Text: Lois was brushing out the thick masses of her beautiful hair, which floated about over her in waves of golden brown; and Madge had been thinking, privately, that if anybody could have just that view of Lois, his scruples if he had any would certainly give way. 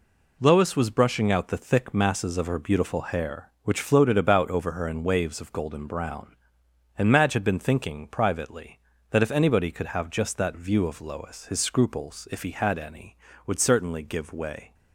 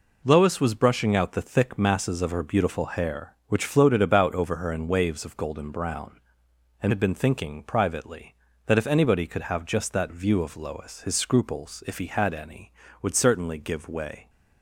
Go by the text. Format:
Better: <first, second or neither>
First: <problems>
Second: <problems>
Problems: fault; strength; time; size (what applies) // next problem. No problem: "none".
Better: first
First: none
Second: skips "Madge"; at 6.9 s